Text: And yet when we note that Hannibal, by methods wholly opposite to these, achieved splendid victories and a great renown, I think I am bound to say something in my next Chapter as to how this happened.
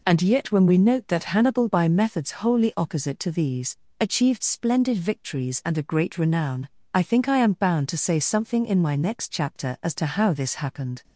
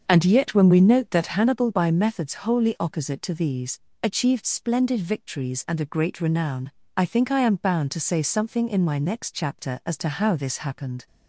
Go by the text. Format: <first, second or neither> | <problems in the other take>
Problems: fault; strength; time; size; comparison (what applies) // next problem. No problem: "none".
first | starts louder than the rest; until 1.3 s; 6.5 dB